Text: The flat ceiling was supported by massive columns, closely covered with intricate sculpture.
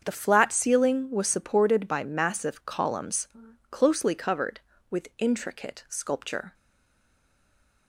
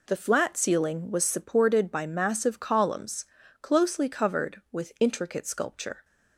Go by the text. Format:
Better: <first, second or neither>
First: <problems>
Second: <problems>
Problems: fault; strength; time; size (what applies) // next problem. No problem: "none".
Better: second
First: starts louder than the rest; until 1.0 s; 7 dB // stays silent after the last word; noticeable; from 6.5 s on; 1.3 s long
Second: none